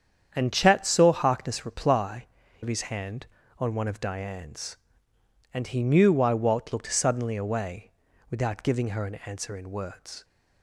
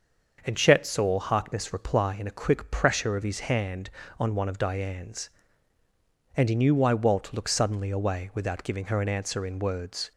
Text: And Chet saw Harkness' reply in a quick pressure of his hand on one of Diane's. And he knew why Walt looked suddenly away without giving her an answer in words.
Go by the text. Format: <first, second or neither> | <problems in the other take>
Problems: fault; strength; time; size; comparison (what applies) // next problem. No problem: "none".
second | starts louder than the rest; strong; until 1.3 s; 8.5 dB; also in the second // skips "in a quick pressure"; at 2.4 s // pauses between "away" and "without"; at 7.9 s; 0.38 s long